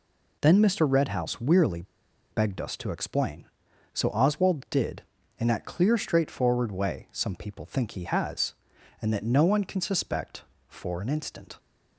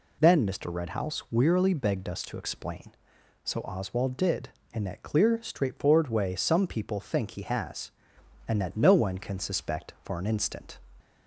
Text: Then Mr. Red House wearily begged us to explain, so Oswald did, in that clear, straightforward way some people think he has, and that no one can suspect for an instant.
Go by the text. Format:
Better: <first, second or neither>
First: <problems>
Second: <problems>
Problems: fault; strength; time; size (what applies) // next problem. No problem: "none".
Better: second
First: pauses between "wearily" and "begged"; noticeable; at 1.8 s; 0.48 s long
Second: none